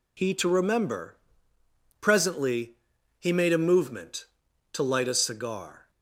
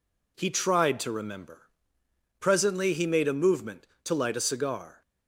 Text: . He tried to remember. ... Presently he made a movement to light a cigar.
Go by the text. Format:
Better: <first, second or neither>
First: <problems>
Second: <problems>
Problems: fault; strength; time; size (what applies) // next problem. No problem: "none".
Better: second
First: skips "tried"; at 0.3 s // pauses between "Presently" and "he"; noticeable; at 2.7 s; 0.46 s long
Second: none